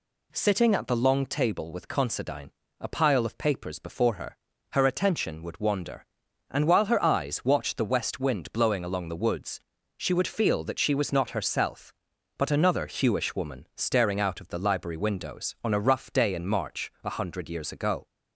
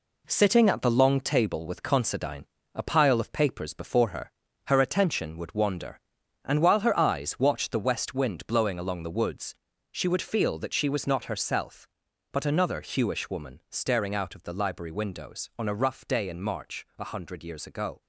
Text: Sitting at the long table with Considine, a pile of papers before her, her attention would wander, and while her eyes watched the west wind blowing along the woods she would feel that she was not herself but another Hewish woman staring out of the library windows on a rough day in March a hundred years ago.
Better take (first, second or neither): first